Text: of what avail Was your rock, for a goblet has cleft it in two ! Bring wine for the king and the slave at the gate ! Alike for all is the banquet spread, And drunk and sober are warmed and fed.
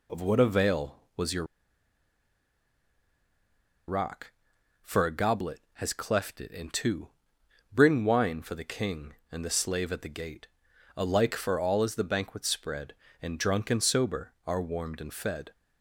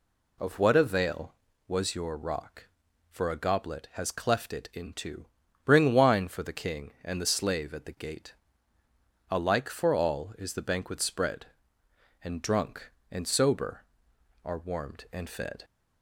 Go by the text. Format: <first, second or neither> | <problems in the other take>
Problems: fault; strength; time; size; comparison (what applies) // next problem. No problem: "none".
second | pauses between "your" and "rock"; strong; at 1.4 s; 2.4 s long